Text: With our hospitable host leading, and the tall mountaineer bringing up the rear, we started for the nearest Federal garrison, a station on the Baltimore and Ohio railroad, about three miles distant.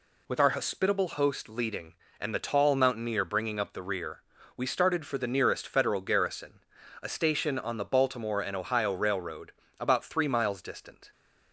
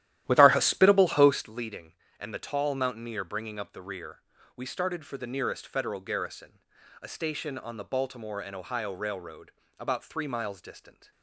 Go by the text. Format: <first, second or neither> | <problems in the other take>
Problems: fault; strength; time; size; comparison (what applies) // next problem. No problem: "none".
first | starts louder than the rest; strong; until 1.6 s; 13 dB